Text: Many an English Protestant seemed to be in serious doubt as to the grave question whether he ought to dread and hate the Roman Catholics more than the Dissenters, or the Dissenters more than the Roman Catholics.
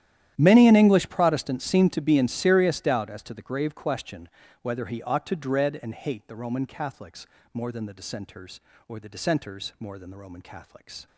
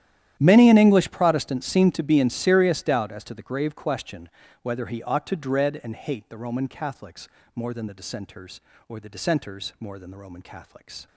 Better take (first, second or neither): neither